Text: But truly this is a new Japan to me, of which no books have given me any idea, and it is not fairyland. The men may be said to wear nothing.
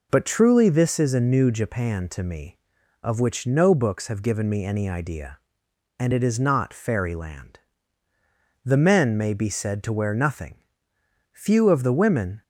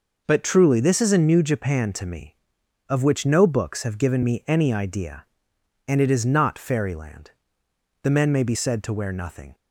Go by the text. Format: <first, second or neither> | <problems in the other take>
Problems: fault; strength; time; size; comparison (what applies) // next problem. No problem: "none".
second | goes on to say "Few of the women"; noticeable; from 11.3 s on; 1.0 s long